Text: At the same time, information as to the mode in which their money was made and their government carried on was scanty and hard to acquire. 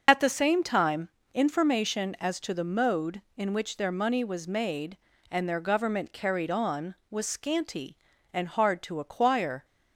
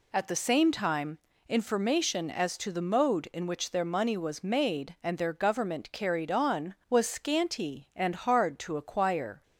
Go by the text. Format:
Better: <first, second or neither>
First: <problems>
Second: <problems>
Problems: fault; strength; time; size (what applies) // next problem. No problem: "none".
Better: second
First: loses the start of "At"; at 0.0 s; 75 ms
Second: none